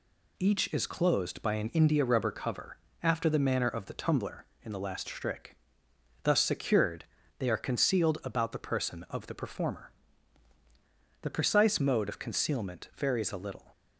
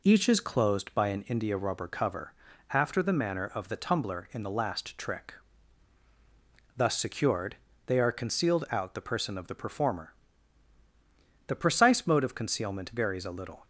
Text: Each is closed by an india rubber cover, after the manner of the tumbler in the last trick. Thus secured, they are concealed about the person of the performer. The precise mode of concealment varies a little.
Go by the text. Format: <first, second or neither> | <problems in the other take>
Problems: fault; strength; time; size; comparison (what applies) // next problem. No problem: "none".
first | says "out" for "about"; at 8.7 s